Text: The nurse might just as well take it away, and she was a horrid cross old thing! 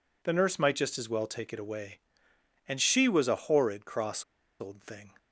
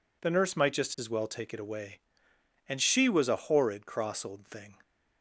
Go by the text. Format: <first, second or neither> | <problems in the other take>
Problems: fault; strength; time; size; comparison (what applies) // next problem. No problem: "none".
second | pauses between "cross" and "old"; at 4.2 s; 0.36 s long